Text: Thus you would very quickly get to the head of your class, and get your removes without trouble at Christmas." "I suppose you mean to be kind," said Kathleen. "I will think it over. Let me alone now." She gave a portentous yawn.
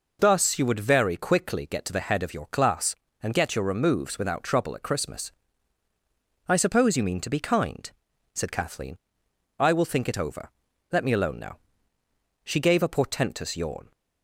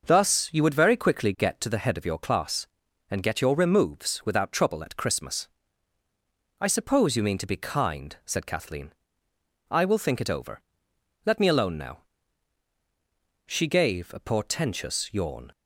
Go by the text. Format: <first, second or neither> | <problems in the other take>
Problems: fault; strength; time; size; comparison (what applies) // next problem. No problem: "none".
neither | none